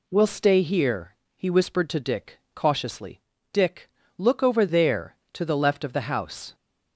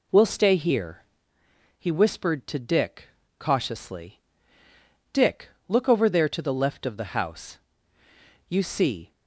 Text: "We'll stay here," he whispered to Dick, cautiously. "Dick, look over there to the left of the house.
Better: first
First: none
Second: goes on to say "You see"; noticeable; from 8.4 s on; 0.64 s long

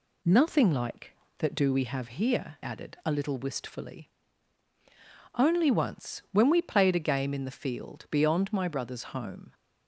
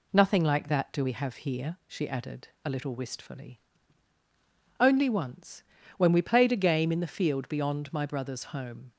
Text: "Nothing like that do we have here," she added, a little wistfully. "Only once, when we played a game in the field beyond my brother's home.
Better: second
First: skips "she"; at 2.6 s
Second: none

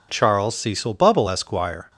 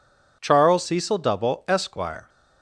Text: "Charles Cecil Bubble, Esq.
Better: first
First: none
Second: says "Double" for "Bubble"; at 1.1 s

